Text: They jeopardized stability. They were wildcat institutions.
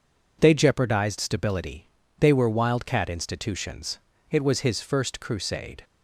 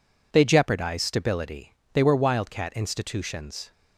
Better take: second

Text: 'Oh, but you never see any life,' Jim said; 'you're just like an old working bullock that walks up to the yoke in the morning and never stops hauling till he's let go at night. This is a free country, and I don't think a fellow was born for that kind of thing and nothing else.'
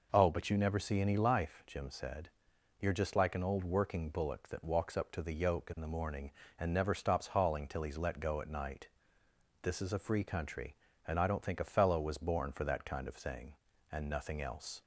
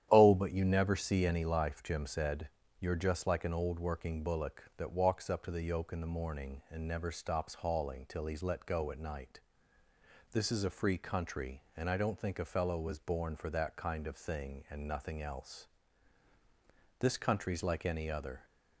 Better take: first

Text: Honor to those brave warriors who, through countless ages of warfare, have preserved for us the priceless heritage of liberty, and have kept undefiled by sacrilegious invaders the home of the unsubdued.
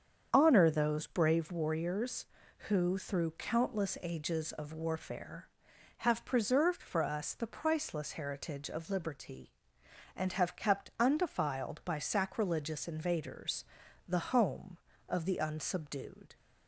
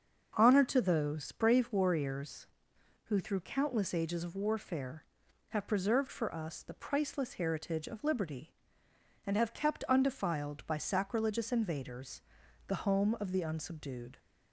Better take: second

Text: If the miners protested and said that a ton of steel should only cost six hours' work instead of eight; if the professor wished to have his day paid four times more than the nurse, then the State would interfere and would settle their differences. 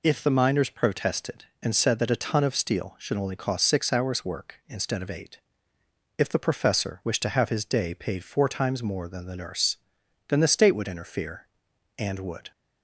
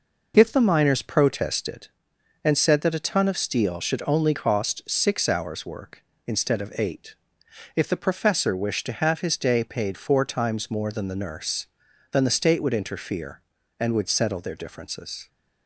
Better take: second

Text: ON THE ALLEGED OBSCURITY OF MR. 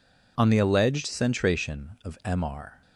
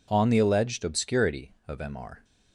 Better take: second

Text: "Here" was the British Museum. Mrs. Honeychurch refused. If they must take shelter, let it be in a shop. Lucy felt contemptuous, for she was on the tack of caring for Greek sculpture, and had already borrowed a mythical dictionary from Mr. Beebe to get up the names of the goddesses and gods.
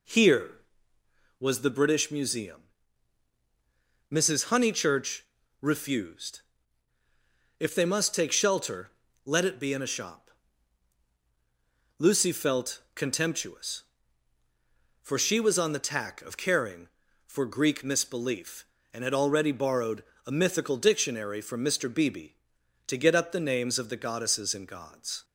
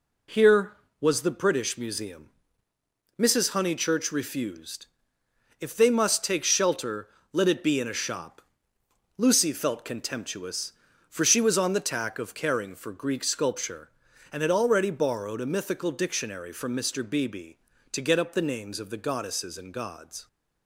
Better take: second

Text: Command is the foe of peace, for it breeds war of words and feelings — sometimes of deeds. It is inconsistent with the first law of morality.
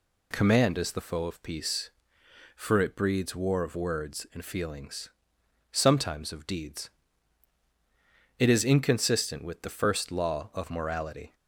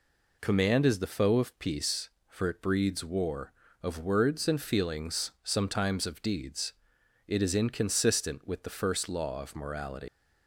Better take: first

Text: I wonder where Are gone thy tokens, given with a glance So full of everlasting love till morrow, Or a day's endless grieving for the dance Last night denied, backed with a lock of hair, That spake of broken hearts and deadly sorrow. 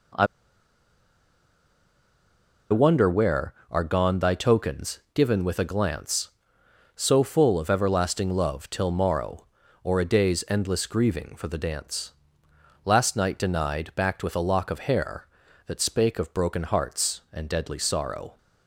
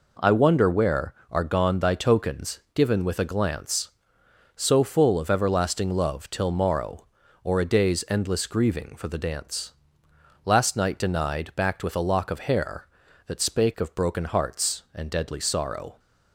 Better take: second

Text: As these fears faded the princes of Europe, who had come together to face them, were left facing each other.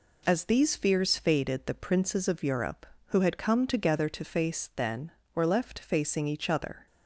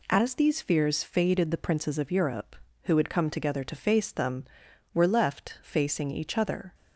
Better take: second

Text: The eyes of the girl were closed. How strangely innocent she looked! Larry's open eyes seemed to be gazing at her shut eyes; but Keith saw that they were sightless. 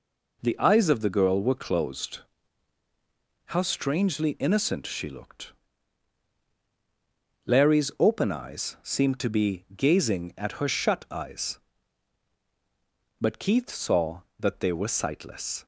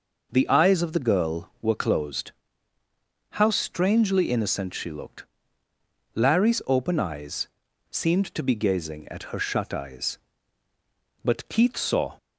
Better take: first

